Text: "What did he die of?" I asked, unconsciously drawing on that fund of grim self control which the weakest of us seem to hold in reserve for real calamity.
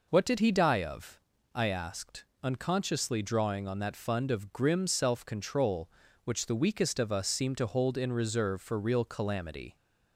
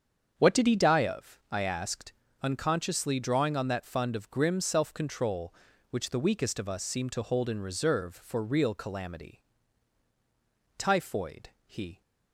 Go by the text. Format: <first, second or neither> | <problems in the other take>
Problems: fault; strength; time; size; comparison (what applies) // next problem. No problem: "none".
first | starts louder than the rest; strong; until 1.3 s; 7.5 dB // goes on to say "Typhoid he"; noticeable; from 10.7 s on; 1.2 s long